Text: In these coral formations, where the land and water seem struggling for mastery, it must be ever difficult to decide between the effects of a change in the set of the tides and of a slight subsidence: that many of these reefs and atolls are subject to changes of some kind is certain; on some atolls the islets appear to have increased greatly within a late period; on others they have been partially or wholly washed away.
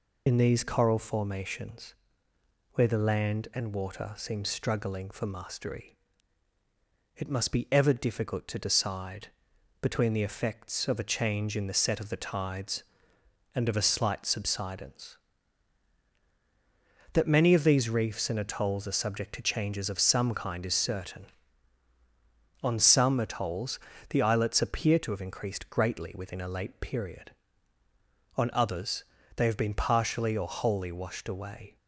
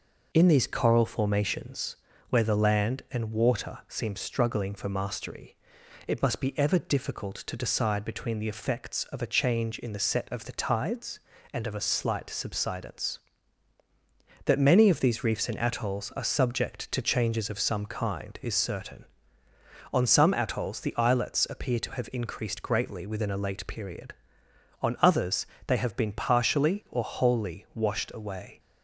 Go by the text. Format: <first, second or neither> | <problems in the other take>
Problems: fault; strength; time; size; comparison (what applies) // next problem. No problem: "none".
second | loses the start of "In"; at 0.2 s; 60 ms // pauses between "decide" and "between"; noticeable; at 9.2 s; 0.56 s long // pauses between "atolls" and "the"; slight; at 23.7 s; 0.30 s long // pauses between "others" and "they"; slight; at 29.0 s; 0.34 s long; slight in the second